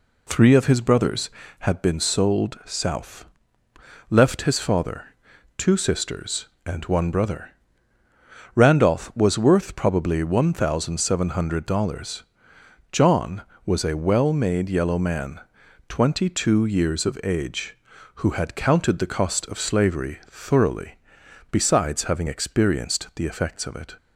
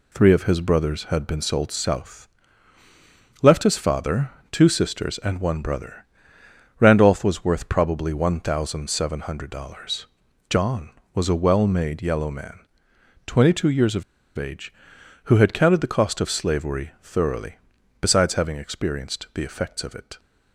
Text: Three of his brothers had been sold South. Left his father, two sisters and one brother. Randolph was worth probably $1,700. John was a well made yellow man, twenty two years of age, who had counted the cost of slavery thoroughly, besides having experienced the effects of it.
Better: first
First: none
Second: pauses between "of" and "age"; slight; at 14.0 s; 0.33 s long

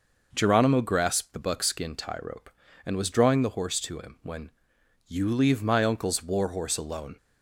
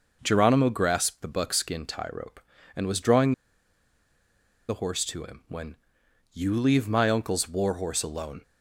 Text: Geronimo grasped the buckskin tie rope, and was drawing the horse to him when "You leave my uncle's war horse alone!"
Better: first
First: pauses between "when" and "You"; noticeable; at 4.5 s; 0.56 s long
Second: pauses between "drawing" and "the"; strong; at 3.3 s; 1.3 s long // pauses between "when" and "You"; noticeable; at 5.7 s; 0.56 s long

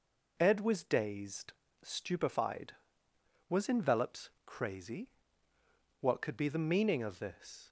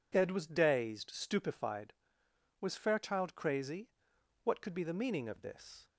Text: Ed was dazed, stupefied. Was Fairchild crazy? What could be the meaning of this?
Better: second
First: says "Envelops" for "Fairchild"; at 3.6 s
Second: none

